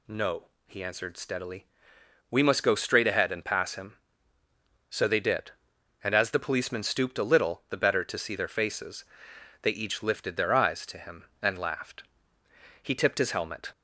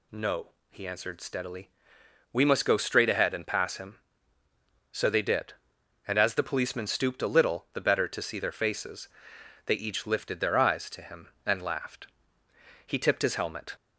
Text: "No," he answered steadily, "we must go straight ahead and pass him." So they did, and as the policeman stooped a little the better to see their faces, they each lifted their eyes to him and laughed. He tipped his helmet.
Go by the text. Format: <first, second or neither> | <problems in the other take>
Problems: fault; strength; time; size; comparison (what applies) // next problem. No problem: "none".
neither | none